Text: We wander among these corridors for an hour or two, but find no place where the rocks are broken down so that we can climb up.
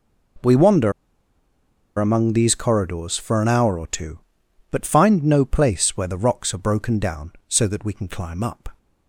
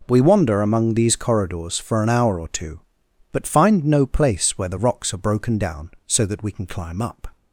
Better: second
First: pauses between "wander" and "among"; at 0.9 s; 1.0 s long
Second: none

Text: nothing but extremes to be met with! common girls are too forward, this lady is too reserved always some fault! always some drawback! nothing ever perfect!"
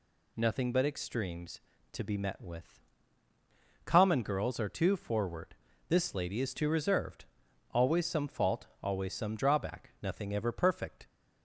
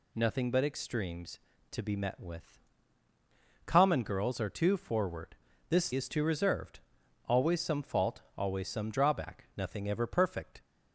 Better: first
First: pauses between "reserved" and "always"; noticeable; at 7.2 s; 0.50 s long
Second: skips "lady"; at 5.9 s // pauses between "reserved" and "always"; noticeable; at 6.7 s; 0.50 s long

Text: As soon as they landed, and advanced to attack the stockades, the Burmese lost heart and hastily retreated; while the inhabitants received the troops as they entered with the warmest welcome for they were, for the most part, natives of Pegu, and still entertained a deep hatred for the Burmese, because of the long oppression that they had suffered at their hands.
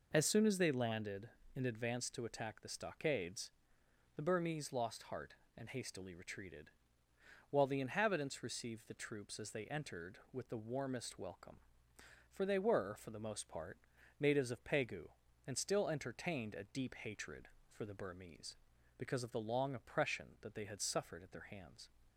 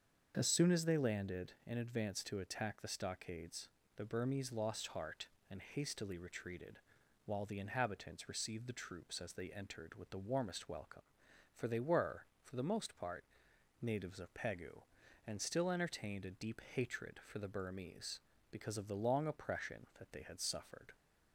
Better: first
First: none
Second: starts louder than the rest; until 1.3 s; 7 dB // stops before "at their hands"; at 20.9 s

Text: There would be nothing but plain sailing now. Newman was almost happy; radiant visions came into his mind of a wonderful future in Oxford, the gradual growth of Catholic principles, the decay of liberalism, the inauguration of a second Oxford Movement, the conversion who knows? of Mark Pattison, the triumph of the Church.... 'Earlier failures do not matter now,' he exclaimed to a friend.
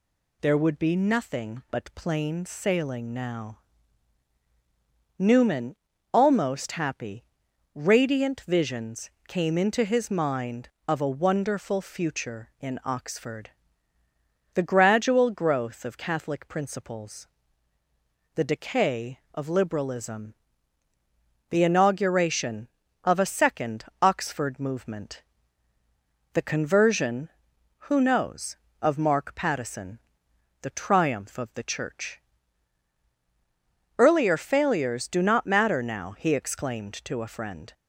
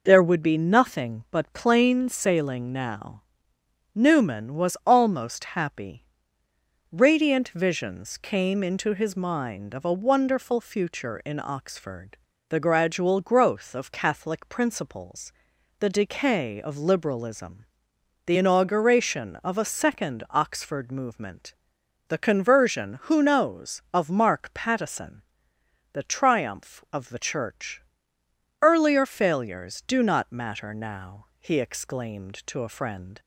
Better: second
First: skips "was"; at 5.9 s // pauses between "visions" and "came"; slight; at 9.0 s; 0.16 s long // pauses between "second" and "Oxford"; slight; at 23.8 s; 0.18 s long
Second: none

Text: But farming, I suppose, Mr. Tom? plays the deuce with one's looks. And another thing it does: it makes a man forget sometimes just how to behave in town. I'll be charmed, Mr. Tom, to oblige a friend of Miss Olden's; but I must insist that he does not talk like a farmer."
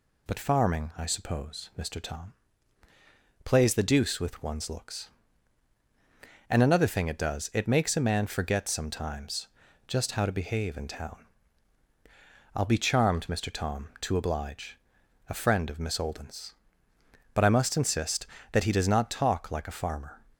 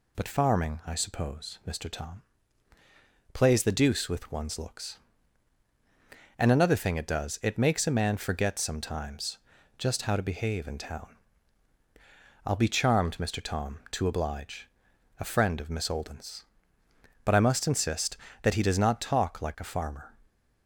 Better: neither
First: pauses between "sometimes" and "just"; at 9.4 s; 0.40 s long // pauses between "oblige" and "a"; noticeable; at 14.7 s; 0.52 s long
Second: pauses between "sometimes" and "just"; at 9.3 s; 0.40 s long // pauses between "oblige" and "a"; noticeable; at 14.6 s; 0.52 s long

